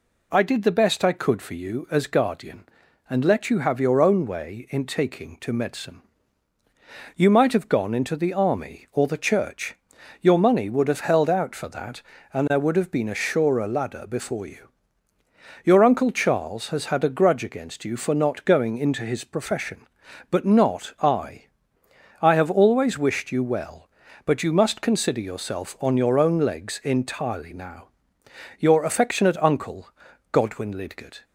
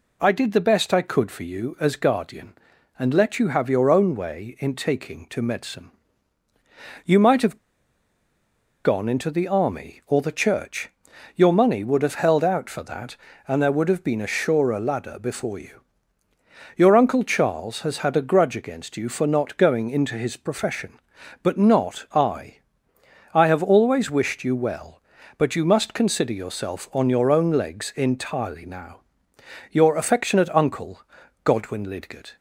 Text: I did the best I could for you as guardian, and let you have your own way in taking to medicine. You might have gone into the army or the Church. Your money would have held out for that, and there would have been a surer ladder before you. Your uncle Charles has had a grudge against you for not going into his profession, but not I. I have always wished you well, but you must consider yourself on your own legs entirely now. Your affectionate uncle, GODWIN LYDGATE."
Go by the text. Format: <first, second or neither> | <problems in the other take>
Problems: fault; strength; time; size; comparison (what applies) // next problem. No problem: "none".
first | pauses between "have" and "gone"; strong; at 7.5 s; 1.2 s long